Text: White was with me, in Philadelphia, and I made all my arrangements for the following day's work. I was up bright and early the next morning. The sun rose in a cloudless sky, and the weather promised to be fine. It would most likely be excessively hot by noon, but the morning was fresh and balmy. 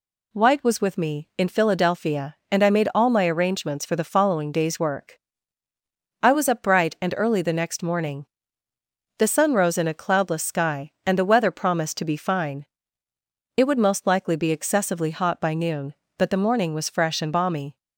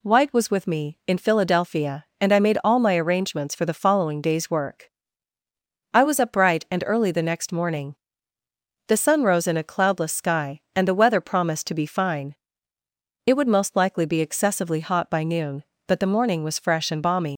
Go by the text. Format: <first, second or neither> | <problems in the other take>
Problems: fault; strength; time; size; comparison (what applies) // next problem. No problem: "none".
first | leaves "balmy" unfinished; at 17.3 s; 125 ms